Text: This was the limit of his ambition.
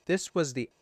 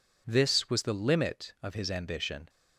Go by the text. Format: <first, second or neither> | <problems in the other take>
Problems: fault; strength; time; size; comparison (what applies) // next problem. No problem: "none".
second | stops before "limit of his ambition"; at 0.6 s